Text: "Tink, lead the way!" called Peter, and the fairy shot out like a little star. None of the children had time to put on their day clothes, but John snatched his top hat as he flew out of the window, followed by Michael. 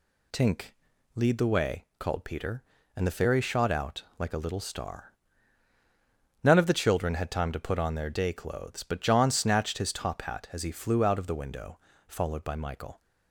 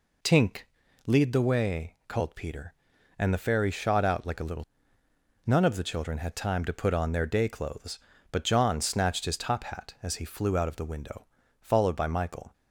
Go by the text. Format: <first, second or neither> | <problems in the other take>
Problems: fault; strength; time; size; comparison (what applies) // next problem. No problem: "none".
first | skips "star"; at 5.0 s